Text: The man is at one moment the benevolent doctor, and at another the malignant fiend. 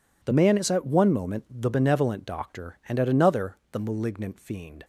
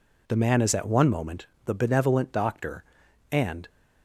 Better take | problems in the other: first | pauses between "moment" and "the"; slight; at 1.4 s; 0.20 s long // stops before "at another the malignant fiend"; at 3.6 s

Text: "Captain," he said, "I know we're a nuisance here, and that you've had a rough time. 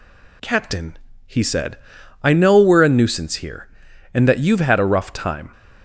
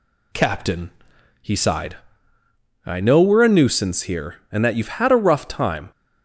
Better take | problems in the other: first | says "sighed" for "said"; at 1.5 s

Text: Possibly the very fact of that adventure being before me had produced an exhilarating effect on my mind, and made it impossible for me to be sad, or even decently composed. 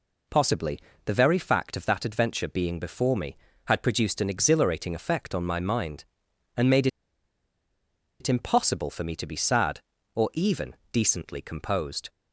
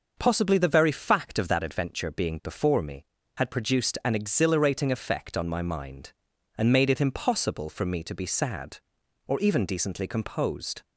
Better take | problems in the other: second | pauses between "Possibly" and "the"; slight; at 0.7 s; 0.26 s long // pauses between "made" and "it"; strong; at 6.8 s; 1.3 s long // pauses between "even" and "decently"; slight; at 10.7 s; 0.16 s long

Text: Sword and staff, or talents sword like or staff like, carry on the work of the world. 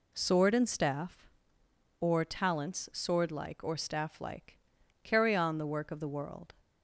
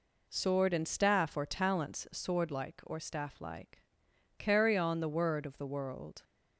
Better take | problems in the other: first | says "word" for "work"; at 5.0 s

